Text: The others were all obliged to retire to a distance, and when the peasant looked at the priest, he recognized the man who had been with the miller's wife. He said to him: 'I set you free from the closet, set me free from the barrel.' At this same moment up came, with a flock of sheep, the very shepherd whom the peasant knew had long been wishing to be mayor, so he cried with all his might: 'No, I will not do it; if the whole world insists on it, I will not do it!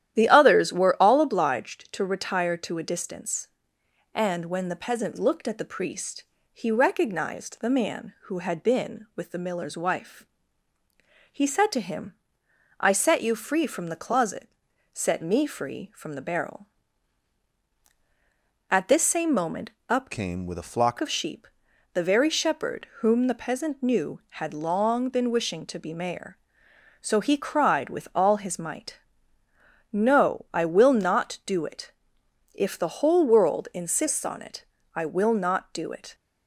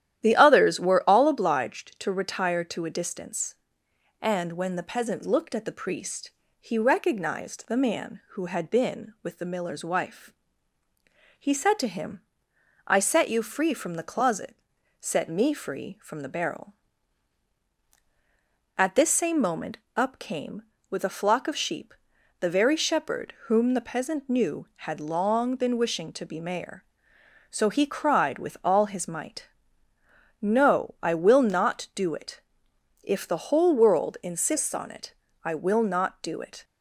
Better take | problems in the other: second | starts louder than the rest; strong; until 1.1 s; 11.5 dB; strong in the second // pauses between "moment" and "up"; slight; at 19.7 s; 0.18 s long; slight in the second // changes voice from "came" to "flock"; from 20.1 to 20.9 s; 0.8 s long

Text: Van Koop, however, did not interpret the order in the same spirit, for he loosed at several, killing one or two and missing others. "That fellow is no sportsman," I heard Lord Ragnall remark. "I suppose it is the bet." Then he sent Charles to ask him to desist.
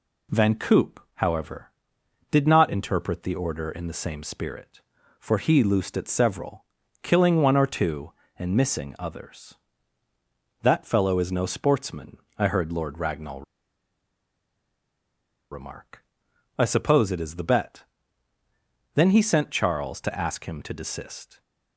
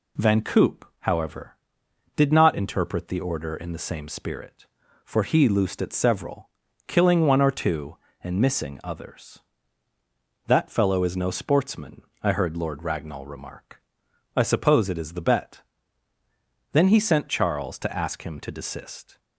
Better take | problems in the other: second | pauses between "Ragnall" and "remark"; strong; at 13.4 s; 2.0 s long

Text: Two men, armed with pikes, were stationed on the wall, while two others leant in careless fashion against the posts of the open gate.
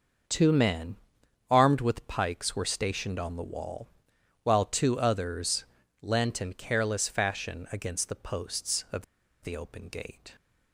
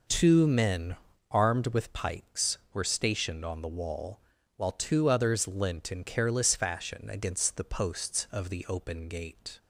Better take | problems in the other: second | starts louder than the rest; until 1.8 s; 6.5 dB // pauses between "others" and "leant"; at 5.6 s; 0.38 s long // pauses between "of" and "the"; at 9.0 s; 0.38 s long

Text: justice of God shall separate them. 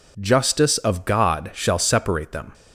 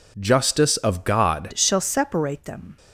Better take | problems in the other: first | changes voice at "shall"; from 1.5 s on; 1.2 s long

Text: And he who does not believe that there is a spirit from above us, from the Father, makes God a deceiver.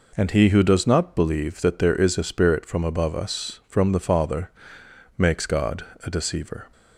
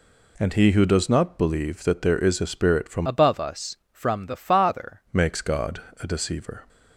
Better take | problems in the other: first | changes voice from "above" to "Father"; from 3.0 to 5.0 s; 2.0 s long // pauses between "God" and "a"; slight; at 5.8 s; 0.18 s long; slight in the first

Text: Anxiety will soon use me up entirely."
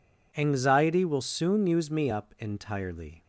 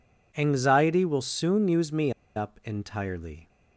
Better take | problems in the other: first | pauses between "me" and "up"; slight; at 2.1 s; 0.24 s long

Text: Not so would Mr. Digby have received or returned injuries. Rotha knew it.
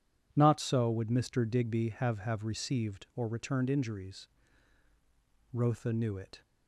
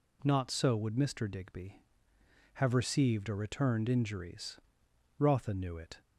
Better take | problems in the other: second | says "have" twice; at 2.1 s

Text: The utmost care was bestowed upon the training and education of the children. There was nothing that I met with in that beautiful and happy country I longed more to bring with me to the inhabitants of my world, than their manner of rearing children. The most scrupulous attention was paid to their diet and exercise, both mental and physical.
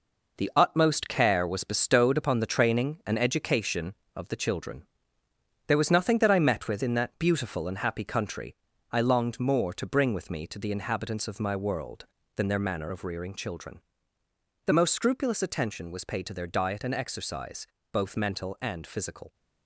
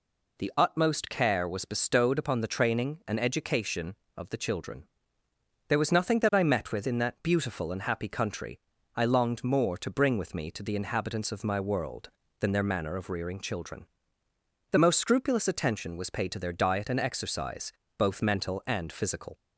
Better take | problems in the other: second | gets quieter; strong; throughout; 7.5 dB // pauses between "country" and "I"; slight; at 8.5 s; 0.34 s long; slight in the second

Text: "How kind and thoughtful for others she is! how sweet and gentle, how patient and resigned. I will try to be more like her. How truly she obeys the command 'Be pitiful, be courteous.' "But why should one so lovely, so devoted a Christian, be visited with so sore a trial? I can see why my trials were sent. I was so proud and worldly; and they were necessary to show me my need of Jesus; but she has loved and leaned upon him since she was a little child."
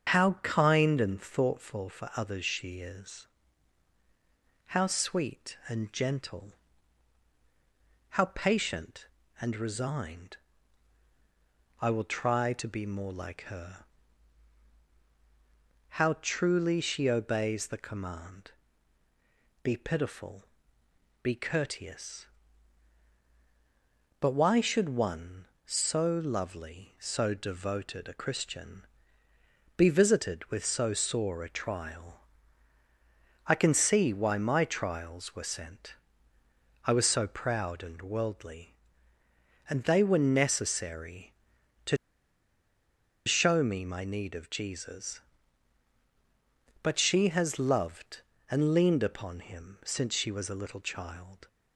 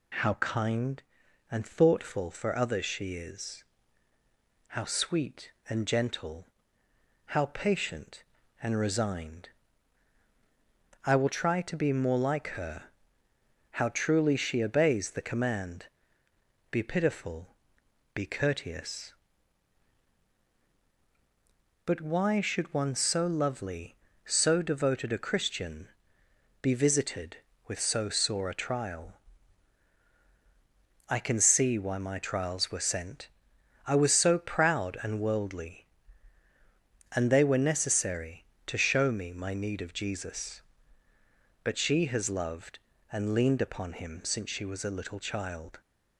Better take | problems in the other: second | starts louder than the rest; until 1.2 s; 6.5 dB // pauses between "command" and "Be"; at 18.5 s; 1.1 s long; noticeable in the second // pauses between "to" and "show"; strong; at 41.9 s; 1.3 s long

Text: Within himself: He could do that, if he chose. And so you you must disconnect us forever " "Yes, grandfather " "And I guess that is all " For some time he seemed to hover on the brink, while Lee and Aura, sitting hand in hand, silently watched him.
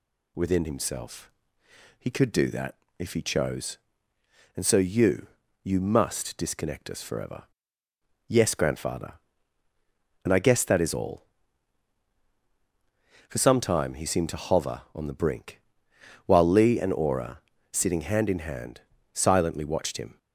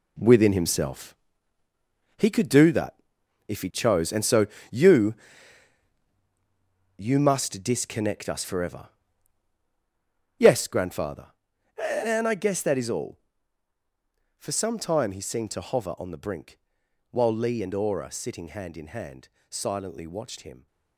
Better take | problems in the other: first | gets quieter; strong; throughout; 11 dB // pauses between "so" and "you"; slight; at 4.4 s; 0.24 s long // pauses between "you" and "you"; strong; at 5.1 s; 1.8 s long; slight in the first

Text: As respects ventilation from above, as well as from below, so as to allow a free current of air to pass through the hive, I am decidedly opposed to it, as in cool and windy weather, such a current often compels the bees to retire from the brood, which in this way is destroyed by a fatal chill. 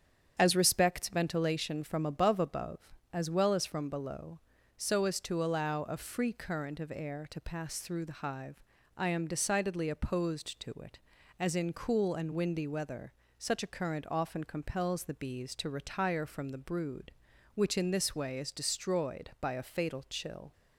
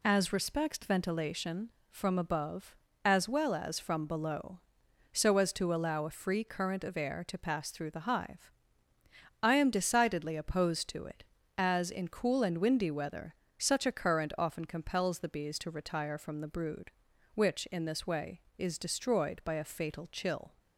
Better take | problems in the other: second | starts louder than the rest; strong; until 1.3 s; 8 dB // says "above" twice; at 2.3 s

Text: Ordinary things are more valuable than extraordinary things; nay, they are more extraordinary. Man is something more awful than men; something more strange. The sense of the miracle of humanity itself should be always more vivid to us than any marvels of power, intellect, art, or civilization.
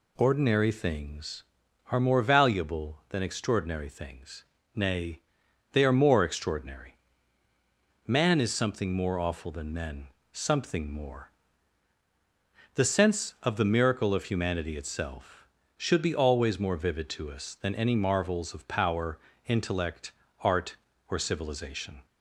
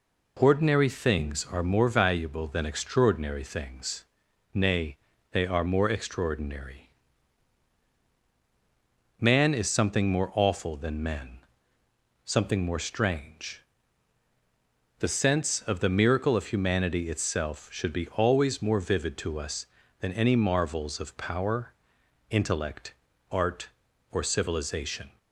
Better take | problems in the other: second | skips "strange"; at 12.0 s

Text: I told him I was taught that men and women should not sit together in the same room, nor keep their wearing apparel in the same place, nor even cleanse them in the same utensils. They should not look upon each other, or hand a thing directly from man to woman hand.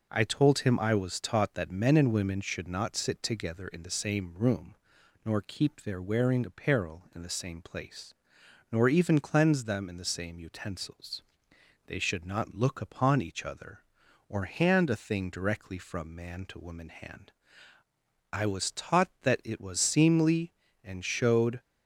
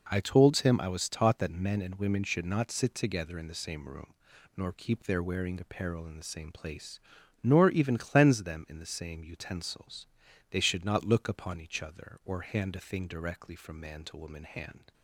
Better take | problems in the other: second | goes on to say "I was taught that it was seemly and showed"; strong; from 18.3 s on; 3.2 s long

